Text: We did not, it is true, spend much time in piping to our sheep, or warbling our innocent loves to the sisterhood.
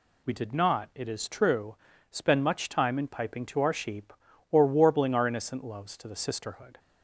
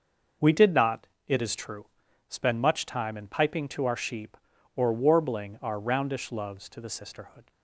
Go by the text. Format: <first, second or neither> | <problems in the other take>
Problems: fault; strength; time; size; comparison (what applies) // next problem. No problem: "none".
first | starts louder than the rest; noticeable; until 1.6 s; 6 dB // says "roundish" for "innocent"; at 5.7 s